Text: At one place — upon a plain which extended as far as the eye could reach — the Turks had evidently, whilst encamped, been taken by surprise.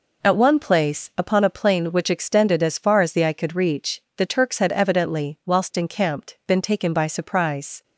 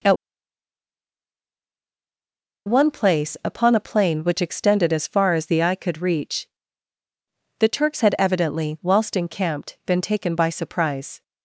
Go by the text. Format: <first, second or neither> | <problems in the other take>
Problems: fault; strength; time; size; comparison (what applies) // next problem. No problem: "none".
first | pauses between "At" and "one"; strong; at 0.1 s; 2.5 s long